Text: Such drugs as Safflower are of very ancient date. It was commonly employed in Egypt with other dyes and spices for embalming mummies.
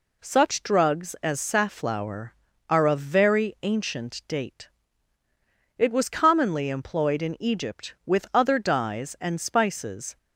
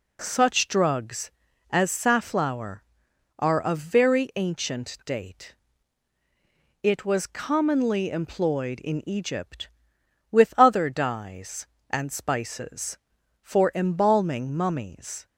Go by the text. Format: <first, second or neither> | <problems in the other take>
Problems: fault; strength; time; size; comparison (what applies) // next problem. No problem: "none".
second | stops before "for embalming mummies"; at 10.1 s